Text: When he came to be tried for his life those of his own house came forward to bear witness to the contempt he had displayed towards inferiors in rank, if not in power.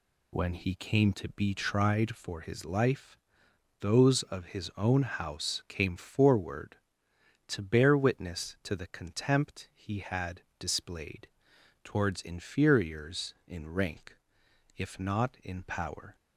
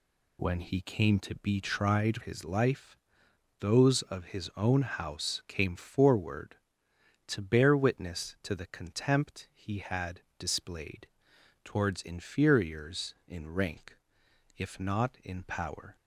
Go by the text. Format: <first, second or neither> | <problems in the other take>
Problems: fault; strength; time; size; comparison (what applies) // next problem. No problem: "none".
first | skips "for"; at 2.2 s // pauses between "life" and "those"; noticeable; at 2.9 s; 0.66 s long; noticeable in the first // pauses between "had" and "displayed"; slight; at 10.2 s; 0.16 s long; slight in the first // pauses between "displayed" and "towards"; noticeable; at 11.0 s; 0.56 s long; noticeable in the first